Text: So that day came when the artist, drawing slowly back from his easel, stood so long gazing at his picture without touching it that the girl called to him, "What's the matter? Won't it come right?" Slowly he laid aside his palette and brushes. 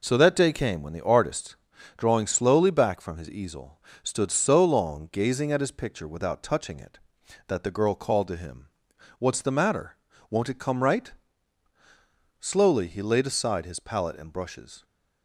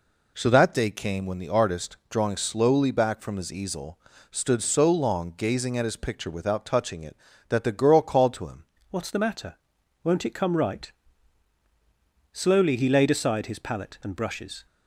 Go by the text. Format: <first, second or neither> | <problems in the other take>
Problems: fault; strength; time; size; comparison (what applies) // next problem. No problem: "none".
first | changes voice at "What's"; from 8.9 s on; 5.7 s long